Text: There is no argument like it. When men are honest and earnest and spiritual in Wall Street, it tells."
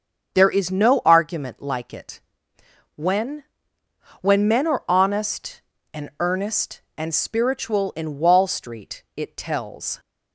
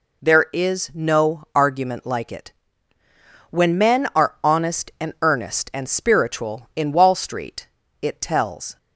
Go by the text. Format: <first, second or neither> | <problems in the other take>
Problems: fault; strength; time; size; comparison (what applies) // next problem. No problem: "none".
second | starts louder than the rest; until 1.3 s; 7 dB // says "When" twice; at 4.2 s